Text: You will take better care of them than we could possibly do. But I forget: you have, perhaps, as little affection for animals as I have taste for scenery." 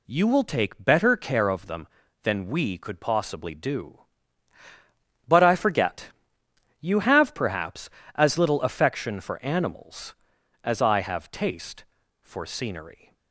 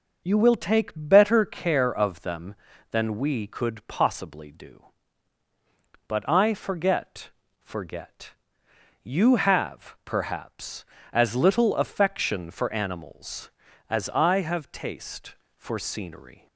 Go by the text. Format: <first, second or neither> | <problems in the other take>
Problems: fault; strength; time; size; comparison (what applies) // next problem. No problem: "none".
first | says "forget" twice; at 7.6 s